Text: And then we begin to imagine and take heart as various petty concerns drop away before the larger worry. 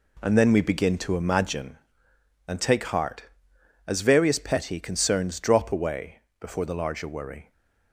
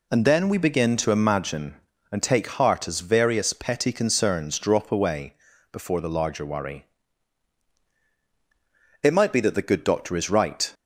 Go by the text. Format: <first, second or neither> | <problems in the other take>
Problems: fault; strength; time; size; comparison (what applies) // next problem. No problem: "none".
first | pauses between "away" and "before"; slight; at 5.3 s; 0.36 s long; slight in the first // goes on to say "It might be that the good doctor is right"; strong; from 9.0 s on; 1.7 s long